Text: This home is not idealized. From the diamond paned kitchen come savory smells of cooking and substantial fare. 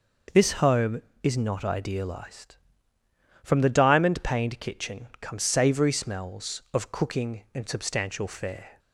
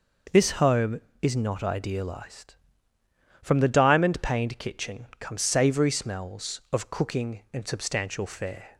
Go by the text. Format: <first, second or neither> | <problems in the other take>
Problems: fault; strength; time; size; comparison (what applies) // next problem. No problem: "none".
neither | none